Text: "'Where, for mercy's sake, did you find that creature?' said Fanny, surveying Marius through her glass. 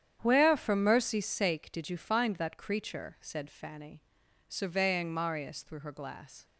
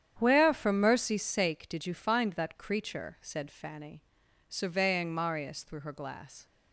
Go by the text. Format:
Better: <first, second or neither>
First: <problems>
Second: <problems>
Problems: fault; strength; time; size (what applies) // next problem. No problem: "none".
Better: neither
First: starts louder than the rest; strong; until 1.2 s; 9 dB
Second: starts louder than the rest; strong; until 1.1 s; 9 dB